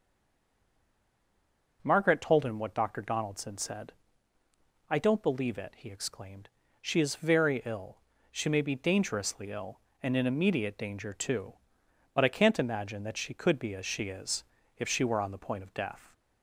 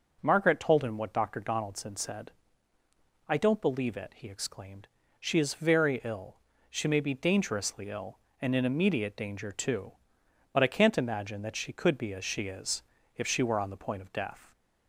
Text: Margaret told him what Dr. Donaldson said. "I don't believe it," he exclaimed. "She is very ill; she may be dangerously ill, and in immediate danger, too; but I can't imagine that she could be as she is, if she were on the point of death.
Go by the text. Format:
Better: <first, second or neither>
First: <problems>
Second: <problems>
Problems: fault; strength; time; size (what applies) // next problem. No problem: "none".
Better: second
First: stays silent before the first word; noticeable; until 1.7 s; 1.7 s long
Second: none